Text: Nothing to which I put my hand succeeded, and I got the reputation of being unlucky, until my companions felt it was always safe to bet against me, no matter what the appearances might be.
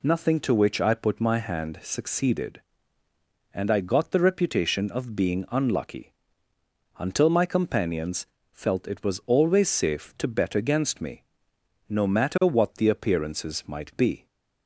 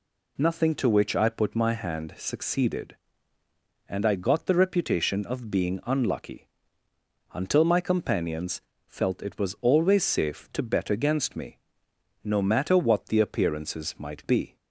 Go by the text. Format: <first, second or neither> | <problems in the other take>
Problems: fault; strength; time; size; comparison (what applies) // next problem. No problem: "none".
neither | pauses between "companions" and "felt"; slight; the same in both